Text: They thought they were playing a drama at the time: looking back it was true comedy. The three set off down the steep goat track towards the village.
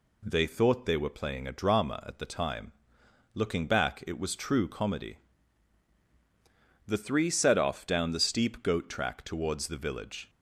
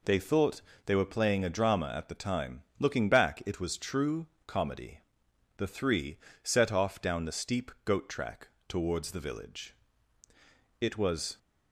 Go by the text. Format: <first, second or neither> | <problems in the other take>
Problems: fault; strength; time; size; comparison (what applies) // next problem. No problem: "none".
first | pauses between "thought" and "they"; slight; at 0.6 s; 0.24 s long // pauses between "true" and "comedy"; slight; at 4.2 s; 0.20 s long // pauses between "three" and "set"; slight; at 6.1 s; 0.24 s long // pauses between "track" and "towards"; slight; at 8.4 s; 0.20 s long // goes on to say "It was"; from 10.8 s on; 0.56 s long